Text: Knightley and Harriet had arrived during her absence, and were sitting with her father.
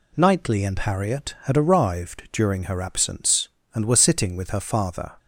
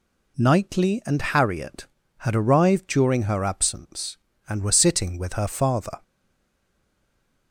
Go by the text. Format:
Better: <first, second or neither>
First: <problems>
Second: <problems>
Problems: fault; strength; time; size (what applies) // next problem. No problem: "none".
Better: first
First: none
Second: stays silent after the last word; noticeable; from 6.0 s on; 1.5 s long